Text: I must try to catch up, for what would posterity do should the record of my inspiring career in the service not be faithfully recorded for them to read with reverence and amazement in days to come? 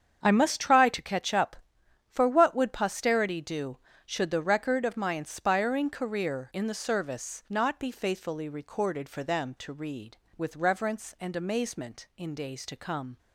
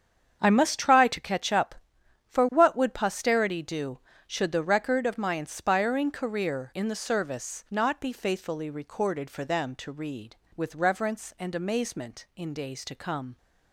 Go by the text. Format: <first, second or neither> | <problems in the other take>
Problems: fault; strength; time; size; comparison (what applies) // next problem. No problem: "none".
neither | starts louder than the rest; strong; the same in both